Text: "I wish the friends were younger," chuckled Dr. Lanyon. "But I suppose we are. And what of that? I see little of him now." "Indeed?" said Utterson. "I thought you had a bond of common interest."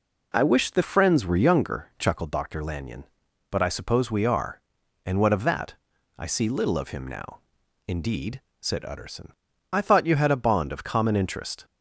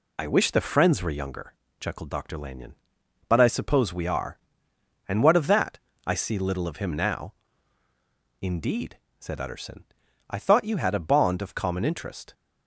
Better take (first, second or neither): neither